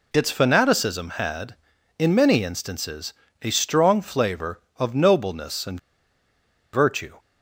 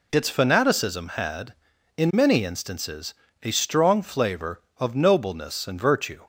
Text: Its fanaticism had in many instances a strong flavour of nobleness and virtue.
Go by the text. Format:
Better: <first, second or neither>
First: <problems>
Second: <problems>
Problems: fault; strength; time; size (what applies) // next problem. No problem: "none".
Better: second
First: pauses between "instances" and "a"; slight; at 3.1 s; 0.28 s long // pauses between "and" and "virtue"; noticeable; at 5.7 s; 0.94 s long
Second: pauses between "instances" and "a"; slight; at 3.1 s; 0.28 s long